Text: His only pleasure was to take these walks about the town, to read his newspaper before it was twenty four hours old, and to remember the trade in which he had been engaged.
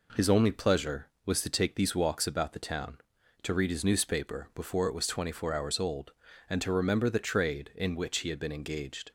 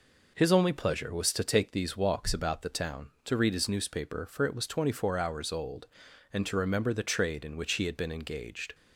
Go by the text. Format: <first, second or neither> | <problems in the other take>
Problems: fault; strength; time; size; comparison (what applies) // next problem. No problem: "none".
first | says "for" for "before"; at 4.2 s